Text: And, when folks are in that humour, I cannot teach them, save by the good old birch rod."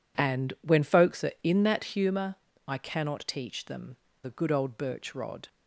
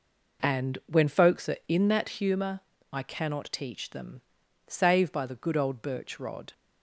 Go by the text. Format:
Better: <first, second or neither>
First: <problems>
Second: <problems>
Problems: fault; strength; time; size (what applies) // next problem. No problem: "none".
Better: second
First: skips "save by"; at 4.0 s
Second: none